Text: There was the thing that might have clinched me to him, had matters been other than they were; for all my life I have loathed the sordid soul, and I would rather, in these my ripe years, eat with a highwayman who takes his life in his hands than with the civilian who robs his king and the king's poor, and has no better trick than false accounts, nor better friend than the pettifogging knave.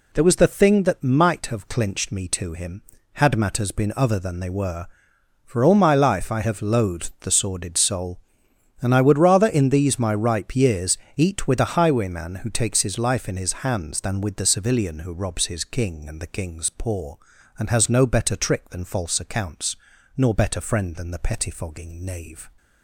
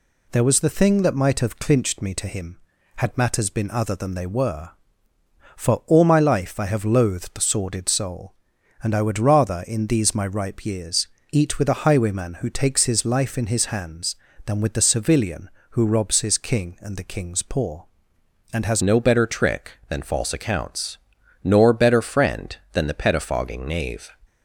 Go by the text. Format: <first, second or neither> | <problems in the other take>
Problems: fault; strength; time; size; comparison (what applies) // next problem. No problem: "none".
first | changes voice at "no"; from 18.8 s on; 5.3 s long